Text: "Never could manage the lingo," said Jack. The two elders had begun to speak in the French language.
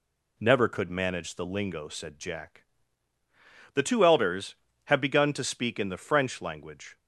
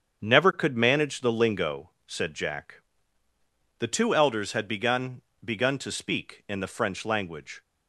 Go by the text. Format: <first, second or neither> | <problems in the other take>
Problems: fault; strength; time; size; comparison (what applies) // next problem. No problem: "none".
first | starts louder than the rest; strong; until 1.2 s; 7.5 dB // says "begun" twice; at 5.4 s